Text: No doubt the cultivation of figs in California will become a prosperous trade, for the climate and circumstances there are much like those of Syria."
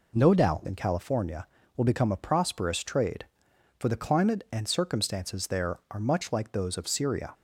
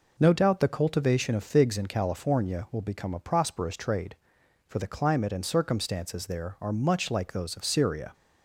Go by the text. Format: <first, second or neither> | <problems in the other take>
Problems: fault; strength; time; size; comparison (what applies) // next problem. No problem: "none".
second | skips "the cultivation of figs"; at 0.6 s